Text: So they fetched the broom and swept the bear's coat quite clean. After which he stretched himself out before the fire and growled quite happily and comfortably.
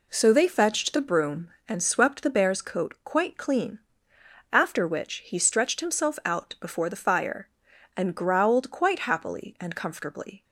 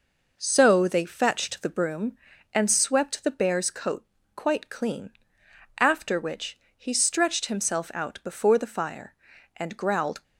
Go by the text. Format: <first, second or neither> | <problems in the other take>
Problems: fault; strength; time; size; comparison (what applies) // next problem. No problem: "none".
first | pauses between "coat" and "quite"; slight; at 4.0 s; 0.30 s long // pauses between "which" and "he"; slight; at 6.5 s; 0.20 s long // stops before "quite happily and comfortably"; at 10.2 s